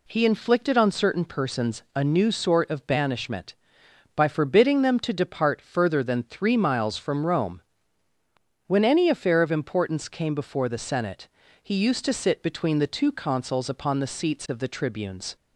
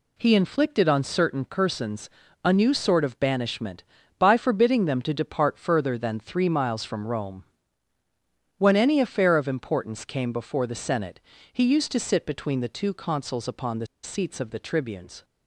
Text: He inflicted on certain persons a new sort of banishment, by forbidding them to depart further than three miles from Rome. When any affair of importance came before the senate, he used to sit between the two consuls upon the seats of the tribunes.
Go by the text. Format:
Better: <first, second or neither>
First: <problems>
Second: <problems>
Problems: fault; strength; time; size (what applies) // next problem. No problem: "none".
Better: first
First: none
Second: pauses between "persons" and "a"; slight; at 2.0 s; 0.34 s long // pauses between "the" and "seats"; slight; at 13.8 s; 0.17 s long